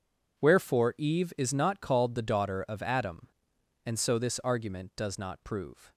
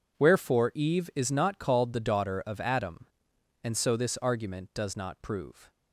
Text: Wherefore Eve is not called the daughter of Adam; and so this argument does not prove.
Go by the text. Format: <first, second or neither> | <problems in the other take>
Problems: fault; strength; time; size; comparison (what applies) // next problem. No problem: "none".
neither | none